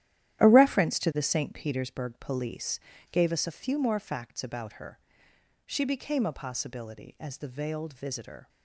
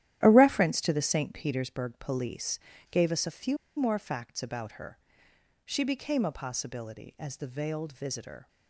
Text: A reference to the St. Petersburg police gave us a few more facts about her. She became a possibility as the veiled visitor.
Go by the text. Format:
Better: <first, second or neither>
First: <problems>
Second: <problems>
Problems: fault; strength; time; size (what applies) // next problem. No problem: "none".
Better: first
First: starts louder than the rest; strong; until 1.4 s; 12.5 dB // pauses between "police" and "gave"; slight; at 2.8 s; 0.32 s long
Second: starts louder than the rest; strong; until 1.2 s; 12 dB // pauses between "police" and "gave"; slight; at 2.5 s; 0.32 s long // pauses between "few" and "more"; slight; at 3.5 s; 0.20 s long